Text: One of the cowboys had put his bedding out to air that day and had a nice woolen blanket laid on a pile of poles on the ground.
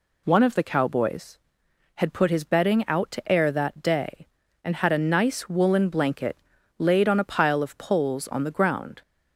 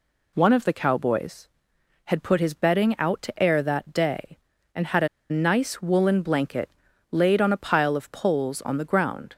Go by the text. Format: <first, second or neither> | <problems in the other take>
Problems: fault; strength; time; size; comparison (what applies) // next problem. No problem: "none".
first | pauses between "a" and "nice"; slight; at 5.0 s; 0.23 s long // pauses between "blanket" and "laid"; at 6.6 s; 0.42 s long; also in the first